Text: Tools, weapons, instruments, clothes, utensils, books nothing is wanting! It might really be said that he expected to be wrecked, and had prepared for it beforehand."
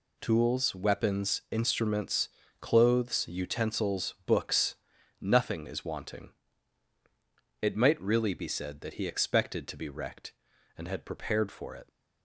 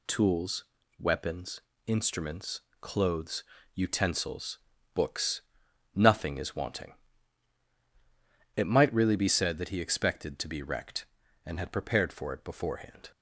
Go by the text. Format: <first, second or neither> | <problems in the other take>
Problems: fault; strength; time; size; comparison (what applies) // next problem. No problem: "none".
second | pauses between "books" and "nothing"; at 4.7 s; 0.44 s long; noticeable in the second // stops before "beforehand"; at 11.8 s